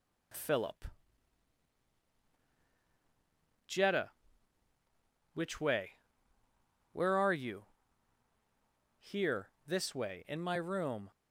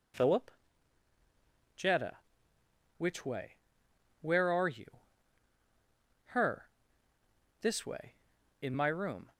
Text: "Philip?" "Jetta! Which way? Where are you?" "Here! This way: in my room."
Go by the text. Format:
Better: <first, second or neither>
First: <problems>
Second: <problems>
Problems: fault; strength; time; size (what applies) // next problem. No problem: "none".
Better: first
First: none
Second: says "Her" for "Here"; at 6.2 s